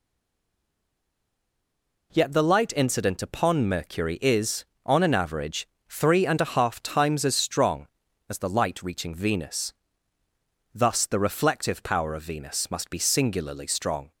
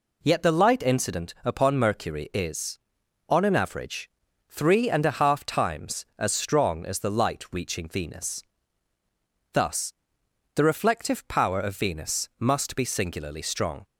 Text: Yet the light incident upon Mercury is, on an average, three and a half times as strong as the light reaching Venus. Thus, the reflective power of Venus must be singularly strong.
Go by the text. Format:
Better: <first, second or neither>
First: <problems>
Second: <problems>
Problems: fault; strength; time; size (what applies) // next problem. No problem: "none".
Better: second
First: stays silent before the first word; noticeable; until 2.1 s; 2.1 s long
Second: none